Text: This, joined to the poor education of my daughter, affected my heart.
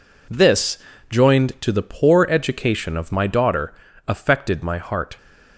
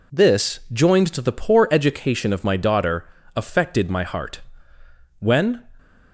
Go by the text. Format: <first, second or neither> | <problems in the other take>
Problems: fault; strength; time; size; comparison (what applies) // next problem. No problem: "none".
first | goes on to say "When"; from 5.1 s on; 0.52 s long